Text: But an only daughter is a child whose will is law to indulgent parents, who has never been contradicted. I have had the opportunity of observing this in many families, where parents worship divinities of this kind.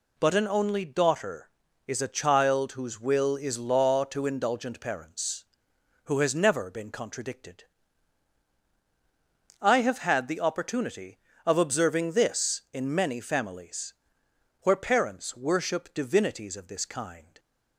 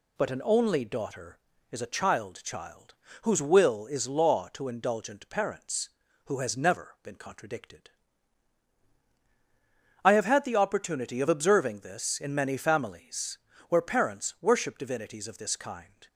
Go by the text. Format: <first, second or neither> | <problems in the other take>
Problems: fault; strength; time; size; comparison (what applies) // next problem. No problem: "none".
first | says "child" twice; at 2.4 s